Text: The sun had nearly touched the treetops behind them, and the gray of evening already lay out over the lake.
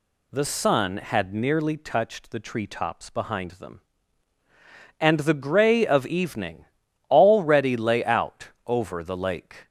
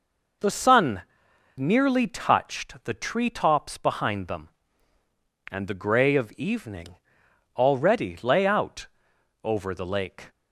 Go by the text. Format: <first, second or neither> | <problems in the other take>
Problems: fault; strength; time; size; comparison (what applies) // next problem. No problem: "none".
first | skips "had"; at 1.3 s // pauses between "evening" and "already"; noticeable; at 6.9 s; 0.58 s long; also in the first // pauses between "out" and "over"; noticeable; at 8.8 s; 0.58 s long; slight in the first